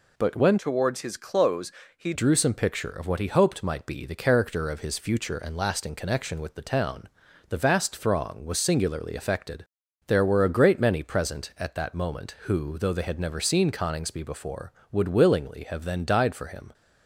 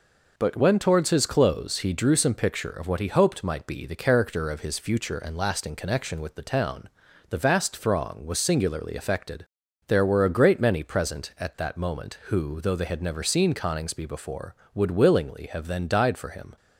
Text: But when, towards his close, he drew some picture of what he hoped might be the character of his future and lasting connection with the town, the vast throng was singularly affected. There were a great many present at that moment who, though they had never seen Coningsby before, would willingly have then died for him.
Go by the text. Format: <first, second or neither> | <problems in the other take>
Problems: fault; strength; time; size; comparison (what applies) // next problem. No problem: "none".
second | changes voice from "towards" to "he"; from 0.5 to 2.1 s; 1.6 s long